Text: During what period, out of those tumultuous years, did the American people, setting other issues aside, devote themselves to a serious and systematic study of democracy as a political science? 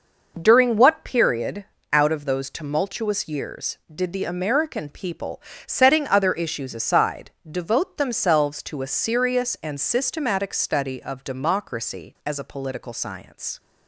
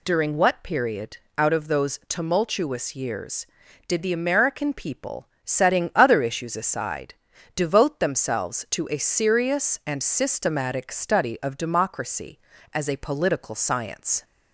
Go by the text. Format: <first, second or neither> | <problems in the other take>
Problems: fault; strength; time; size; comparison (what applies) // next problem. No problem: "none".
neither | none